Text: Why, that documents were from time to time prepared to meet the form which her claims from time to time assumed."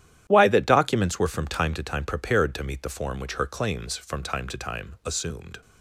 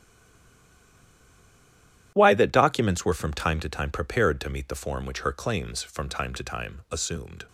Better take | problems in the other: first | stays silent before the first word; until 2.1 s; 2.1 s long // starts louder than the rest; strong; until 3.1 s; 11.5 dB; strong in the first

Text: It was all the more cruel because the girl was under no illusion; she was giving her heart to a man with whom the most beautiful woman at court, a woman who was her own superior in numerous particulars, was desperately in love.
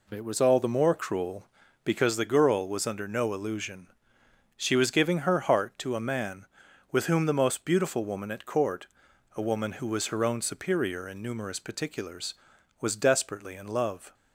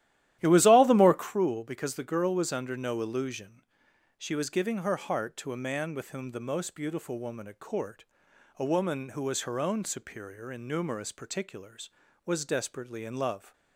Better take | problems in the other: first | starts louder than the rest; strong; until 1.3 s; 13 dB

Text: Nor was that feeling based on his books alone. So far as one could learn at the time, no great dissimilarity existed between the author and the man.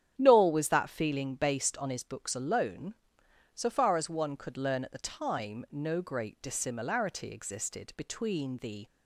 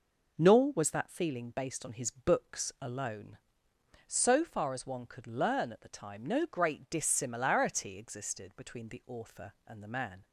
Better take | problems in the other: second | starts louder than the rest; strong; until 1.1 s; 9.5 dB // stops before "author and the man"; at 8.8 s

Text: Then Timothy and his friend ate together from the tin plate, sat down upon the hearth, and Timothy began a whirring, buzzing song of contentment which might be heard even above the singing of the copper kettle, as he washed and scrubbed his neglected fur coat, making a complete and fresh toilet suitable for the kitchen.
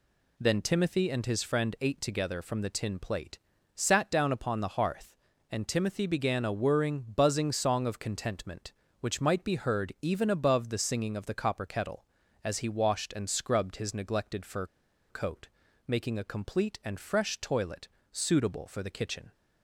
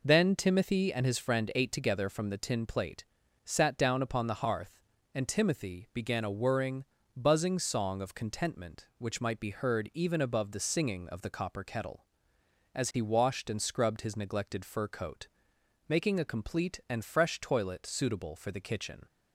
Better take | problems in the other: second | pauses between "fur" and "coat"; at 14.6 s; 0.45 s long // pauses between "toilet" and "suitable"; slight; at 17.8 s; 0.24 s long

